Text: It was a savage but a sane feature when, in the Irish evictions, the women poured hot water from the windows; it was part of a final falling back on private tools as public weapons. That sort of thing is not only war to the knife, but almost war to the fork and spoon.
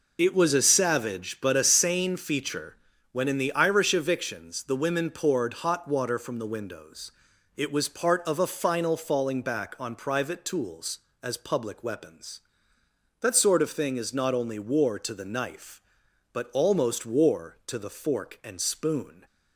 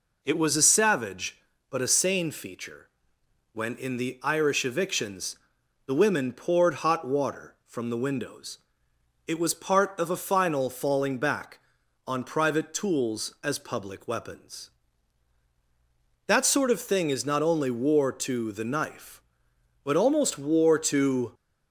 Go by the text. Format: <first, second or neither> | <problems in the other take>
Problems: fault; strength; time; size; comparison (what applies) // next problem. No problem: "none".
first | pauses between "feature" and "when"; noticeable; at 2.8 s; 0.66 s long; slight in the first // stops before "the fork and spoon"; at 21.3 s